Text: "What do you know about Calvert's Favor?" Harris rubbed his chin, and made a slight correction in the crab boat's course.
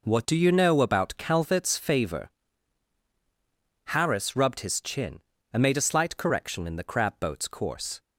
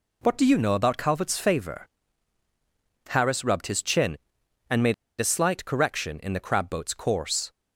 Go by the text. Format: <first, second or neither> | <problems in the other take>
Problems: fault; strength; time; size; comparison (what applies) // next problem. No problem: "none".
first | pauses between "made" and "a"; slight; at 4.9 s; 0.24 s long